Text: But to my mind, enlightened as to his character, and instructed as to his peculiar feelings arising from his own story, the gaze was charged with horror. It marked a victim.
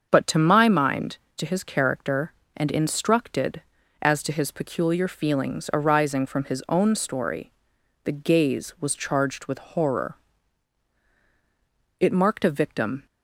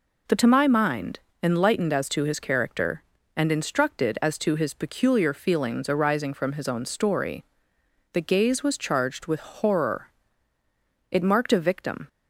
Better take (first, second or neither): second